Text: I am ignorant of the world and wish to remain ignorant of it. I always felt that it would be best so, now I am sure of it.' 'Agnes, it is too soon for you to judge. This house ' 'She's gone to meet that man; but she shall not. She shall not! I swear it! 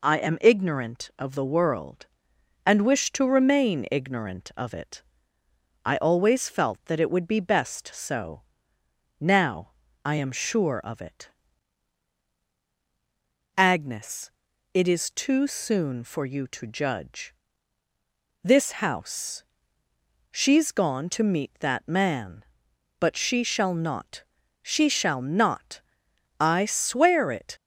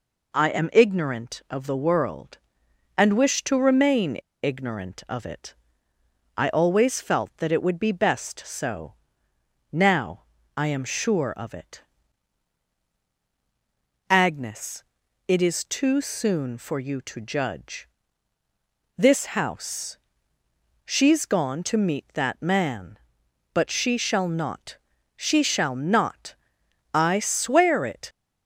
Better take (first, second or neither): first